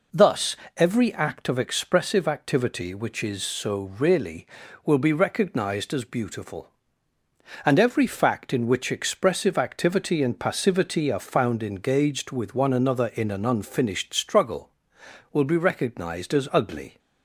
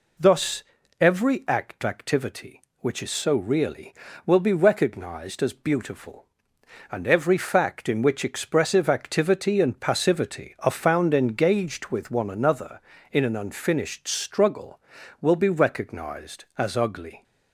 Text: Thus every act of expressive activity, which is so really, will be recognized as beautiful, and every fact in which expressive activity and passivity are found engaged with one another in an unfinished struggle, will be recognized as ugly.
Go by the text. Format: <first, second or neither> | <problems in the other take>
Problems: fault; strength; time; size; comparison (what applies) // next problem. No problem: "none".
first | pauses between "Thus" and "every"; slight; at 0.6 s; 0.36 s long; slight in the first // skips "of expressive"; at 1.8 s